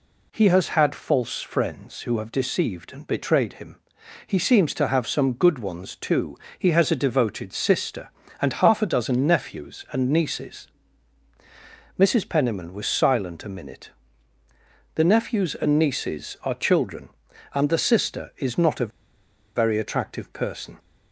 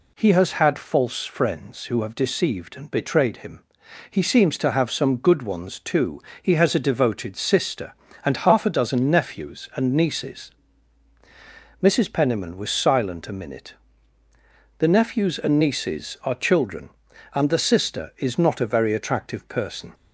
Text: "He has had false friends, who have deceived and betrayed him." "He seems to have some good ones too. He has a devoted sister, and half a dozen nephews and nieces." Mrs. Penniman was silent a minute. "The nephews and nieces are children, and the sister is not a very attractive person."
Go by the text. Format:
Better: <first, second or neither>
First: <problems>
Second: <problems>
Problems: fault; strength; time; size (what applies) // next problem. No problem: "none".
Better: second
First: pauses between "a" and "very"; noticeable; at 18.9 s; 0.65 s long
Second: none